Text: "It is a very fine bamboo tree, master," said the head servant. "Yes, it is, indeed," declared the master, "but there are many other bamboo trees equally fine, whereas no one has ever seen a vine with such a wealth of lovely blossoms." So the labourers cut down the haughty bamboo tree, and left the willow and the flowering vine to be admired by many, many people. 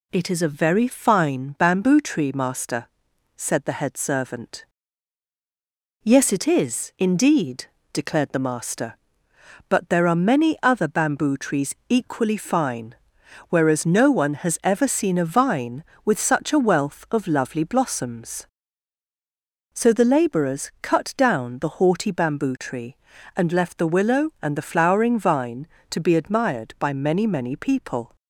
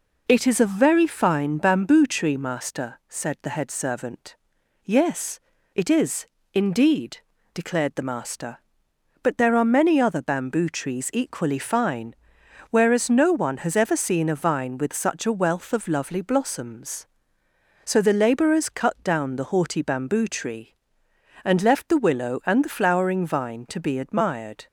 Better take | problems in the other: first | stops before "by many many people"; at 24.6 s

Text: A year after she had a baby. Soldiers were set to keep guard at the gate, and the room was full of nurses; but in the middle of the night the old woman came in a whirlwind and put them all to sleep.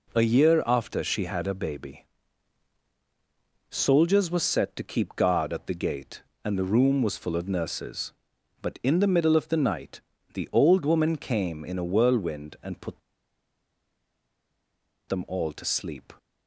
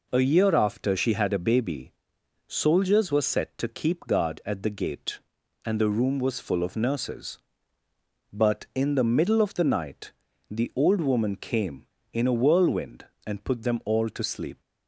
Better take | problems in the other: second | pauses between "night" and "the"; slight; at 10.0 s; 0.32 s long; slight in the second // pauses between "put" and "them"; strong; at 13.0 s; 2.1 s long

